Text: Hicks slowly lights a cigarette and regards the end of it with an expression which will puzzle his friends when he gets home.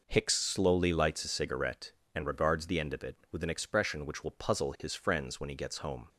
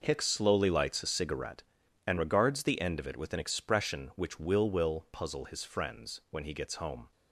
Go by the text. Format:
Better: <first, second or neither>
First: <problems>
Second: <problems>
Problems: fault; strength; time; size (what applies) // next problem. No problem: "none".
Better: first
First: none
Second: says "will" twice; at 4.7 s